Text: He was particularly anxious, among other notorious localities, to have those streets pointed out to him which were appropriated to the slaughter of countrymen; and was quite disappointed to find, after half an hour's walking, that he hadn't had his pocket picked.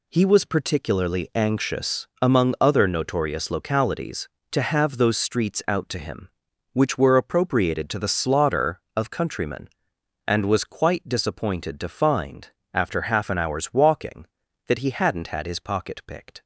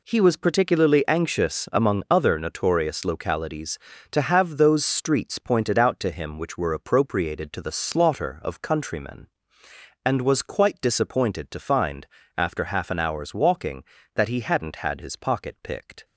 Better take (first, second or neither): second